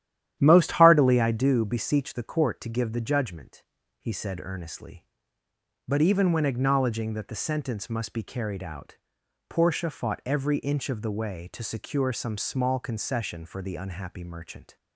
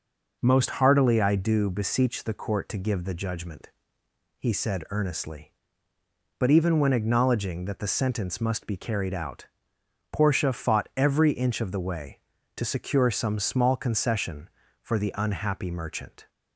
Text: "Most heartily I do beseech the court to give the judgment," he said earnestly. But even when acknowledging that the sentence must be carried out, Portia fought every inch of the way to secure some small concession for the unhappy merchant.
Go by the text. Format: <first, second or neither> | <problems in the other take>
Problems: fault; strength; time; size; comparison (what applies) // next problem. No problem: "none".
second | starts louder than the rest; strong; until 1.5 s; 11.5 dB